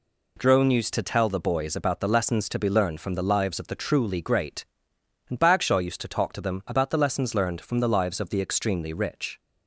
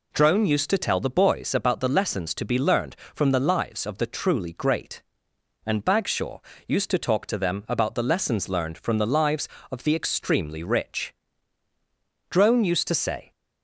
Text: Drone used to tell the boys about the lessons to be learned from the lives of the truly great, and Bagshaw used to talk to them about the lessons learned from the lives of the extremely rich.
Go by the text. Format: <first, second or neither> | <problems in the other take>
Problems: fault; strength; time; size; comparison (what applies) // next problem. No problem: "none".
first | pauses between "Bagshaw" and "used"; slight; at 6.3 s; 0.28 s long // goes on to say "Drone used to say"; noticeable; from 12.2 s on; 1.0 s long